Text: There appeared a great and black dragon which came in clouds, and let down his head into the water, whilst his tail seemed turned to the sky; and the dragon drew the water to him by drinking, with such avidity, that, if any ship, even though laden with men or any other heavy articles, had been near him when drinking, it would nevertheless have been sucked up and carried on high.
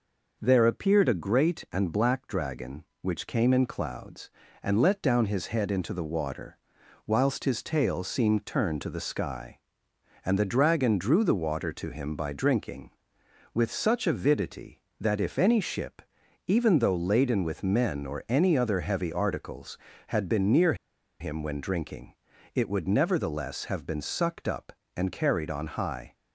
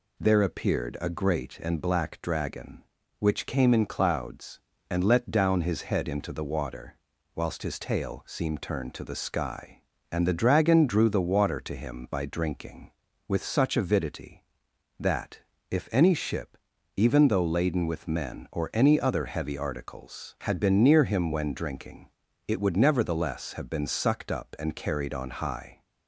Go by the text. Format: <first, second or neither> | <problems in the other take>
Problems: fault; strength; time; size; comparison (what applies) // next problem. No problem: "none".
second | pauses between "near" and "him"; noticeable; at 20.7 s; 0.46 s long